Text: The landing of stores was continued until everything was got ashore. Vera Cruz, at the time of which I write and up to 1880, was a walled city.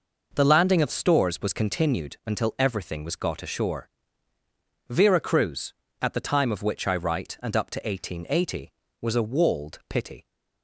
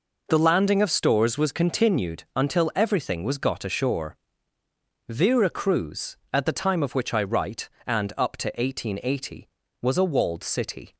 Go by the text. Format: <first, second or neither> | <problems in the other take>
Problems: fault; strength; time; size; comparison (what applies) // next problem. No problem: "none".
second | says "pity" for "city"; at 9.9 s